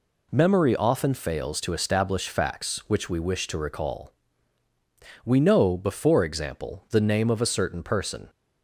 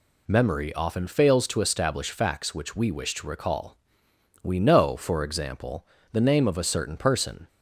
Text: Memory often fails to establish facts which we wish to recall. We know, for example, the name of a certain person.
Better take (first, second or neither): second